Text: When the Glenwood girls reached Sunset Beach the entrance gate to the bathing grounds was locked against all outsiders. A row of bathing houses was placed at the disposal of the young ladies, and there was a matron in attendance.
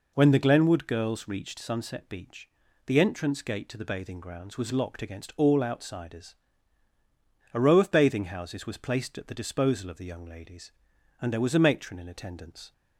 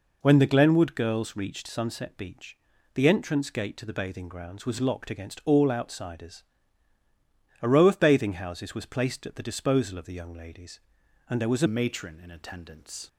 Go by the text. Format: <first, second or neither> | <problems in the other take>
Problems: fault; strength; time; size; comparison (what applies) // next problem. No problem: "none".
first | pauses between "Beach" and "the"; at 2.5 s; 0.38 s long; also in the first // changes voice at "matron"; from 11.6 s on; 1.4 s long